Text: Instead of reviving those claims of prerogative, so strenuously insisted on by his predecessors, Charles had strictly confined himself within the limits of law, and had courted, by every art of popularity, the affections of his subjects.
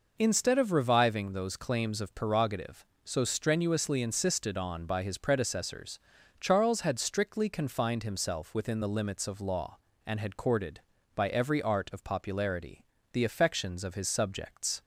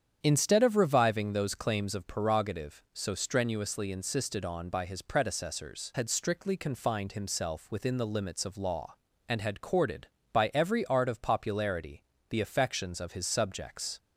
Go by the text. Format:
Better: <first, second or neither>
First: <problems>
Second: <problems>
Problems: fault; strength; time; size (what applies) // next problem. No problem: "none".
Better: first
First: none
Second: starts louder than the rest; strong; until 1.2 s; 8.5 dB // skips "Charles"; at 5.9 s